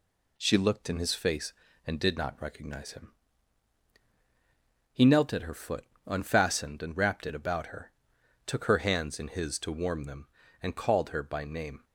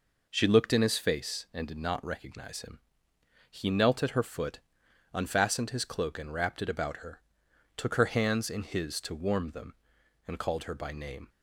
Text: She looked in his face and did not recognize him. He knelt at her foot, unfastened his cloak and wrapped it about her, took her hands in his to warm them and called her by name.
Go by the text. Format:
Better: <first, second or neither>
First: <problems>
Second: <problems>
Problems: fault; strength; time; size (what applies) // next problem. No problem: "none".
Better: second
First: skips "his cloak"; at 6.8 s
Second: none